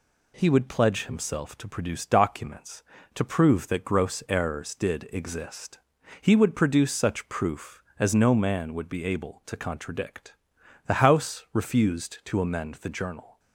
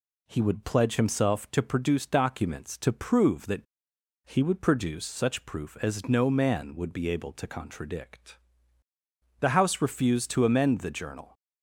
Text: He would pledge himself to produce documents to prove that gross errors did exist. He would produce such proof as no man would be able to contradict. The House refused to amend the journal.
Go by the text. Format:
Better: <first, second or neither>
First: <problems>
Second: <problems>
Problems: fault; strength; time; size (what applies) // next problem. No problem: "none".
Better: first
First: none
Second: skips "gross errors did exist"; at 3.9 s